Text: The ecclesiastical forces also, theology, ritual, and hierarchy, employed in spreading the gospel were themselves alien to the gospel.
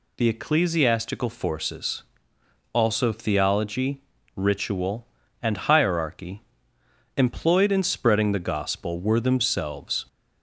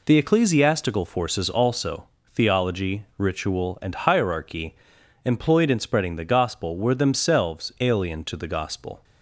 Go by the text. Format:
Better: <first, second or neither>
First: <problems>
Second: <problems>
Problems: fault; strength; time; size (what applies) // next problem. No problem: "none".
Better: second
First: pauses between "forces" and "also"; noticeable; at 2.0 s; 0.70 s long // stops before "alien to the gospel"; at 10.0 s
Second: none